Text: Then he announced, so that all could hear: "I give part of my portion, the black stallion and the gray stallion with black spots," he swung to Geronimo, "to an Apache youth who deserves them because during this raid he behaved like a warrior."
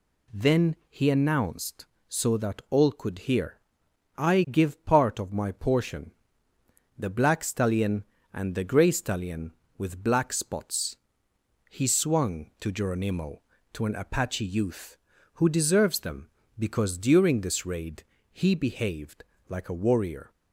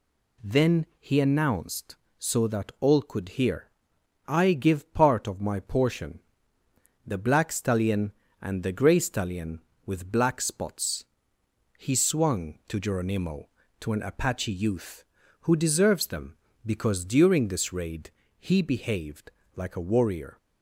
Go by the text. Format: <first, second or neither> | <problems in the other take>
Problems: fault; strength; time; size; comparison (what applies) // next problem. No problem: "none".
neither | pauses between "raid" and "he"; slight; the same in both // pauses between "behaved" and "like"; slight; the same in both